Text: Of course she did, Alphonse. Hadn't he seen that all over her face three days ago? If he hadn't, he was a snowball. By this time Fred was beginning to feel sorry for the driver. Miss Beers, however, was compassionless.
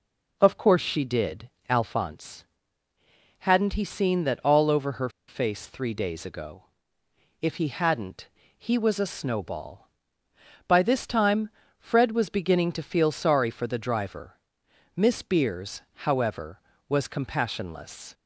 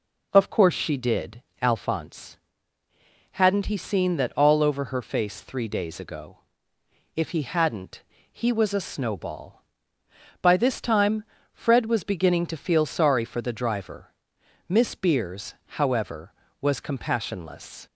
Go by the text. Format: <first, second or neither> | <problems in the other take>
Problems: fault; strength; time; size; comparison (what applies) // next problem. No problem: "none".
second | pauses between "her" and "face"; slight; at 5.0 s; 0.19 s long // pauses between "time" and "Fred"; slight; at 11.4 s; 0.30 s long; slight in the second